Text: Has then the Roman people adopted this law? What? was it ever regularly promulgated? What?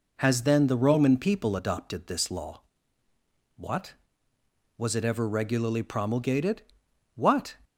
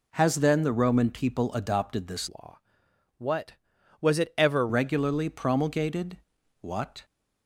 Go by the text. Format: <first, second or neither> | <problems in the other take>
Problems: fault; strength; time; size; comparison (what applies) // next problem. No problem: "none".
first | changes voice from "law" to "ever"; from 2.2 to 4.6 s; 2.4 s long